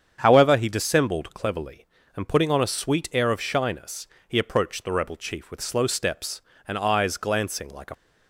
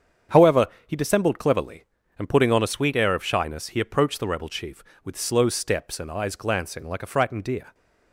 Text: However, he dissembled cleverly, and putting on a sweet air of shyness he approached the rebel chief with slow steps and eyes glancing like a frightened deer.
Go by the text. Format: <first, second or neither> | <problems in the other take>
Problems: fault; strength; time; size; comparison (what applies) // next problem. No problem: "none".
second | starts louder than the rest; strong; until 1.2 s; 7.5 dB; strong in the second // pauses between "shyness" and "he"; slight; at 4.0 s; 0.22 s long // stops before "frightened deer"; at 7.9 s